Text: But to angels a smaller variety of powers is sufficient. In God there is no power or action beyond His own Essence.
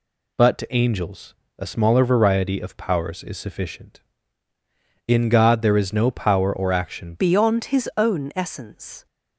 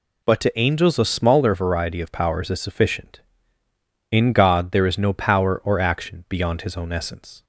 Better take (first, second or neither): second